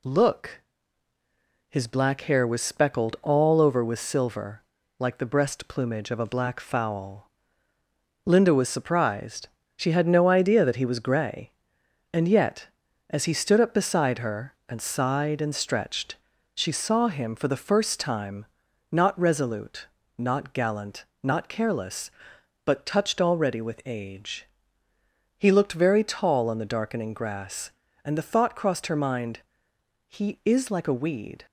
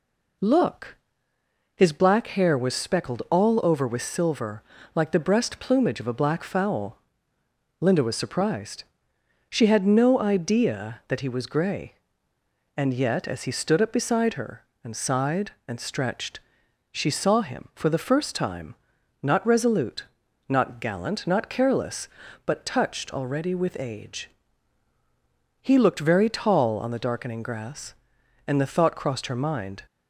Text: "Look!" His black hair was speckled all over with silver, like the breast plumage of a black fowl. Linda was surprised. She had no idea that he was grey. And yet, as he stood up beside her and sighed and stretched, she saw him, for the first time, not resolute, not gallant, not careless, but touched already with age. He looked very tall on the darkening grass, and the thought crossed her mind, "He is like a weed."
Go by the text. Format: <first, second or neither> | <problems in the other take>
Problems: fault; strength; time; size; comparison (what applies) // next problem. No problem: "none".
first | stops before "He is like a weed"; at 29.8 s